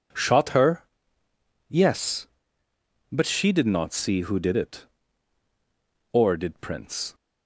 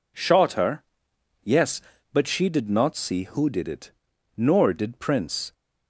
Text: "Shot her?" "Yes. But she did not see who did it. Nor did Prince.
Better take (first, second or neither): second